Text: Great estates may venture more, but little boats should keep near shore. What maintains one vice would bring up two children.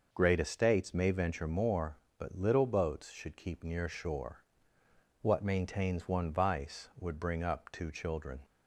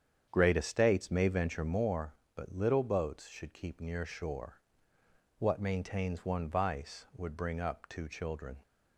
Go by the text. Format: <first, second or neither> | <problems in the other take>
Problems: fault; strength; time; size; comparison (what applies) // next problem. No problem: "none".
first | starts louder than the rest; strong; until 2.0 s; 8 dB